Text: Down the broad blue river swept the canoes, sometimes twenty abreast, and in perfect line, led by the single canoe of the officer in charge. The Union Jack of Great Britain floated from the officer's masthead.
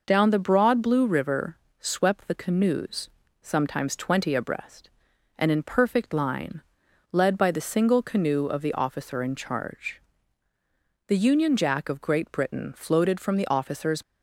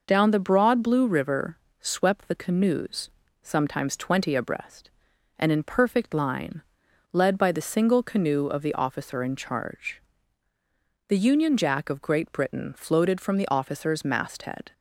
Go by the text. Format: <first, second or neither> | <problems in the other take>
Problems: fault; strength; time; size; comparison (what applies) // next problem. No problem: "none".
second | pauses between "river" and "swept"; slight; at 1.5 s; 0.24 s long; slight in the second // stops before "masthead"; at 14.0 s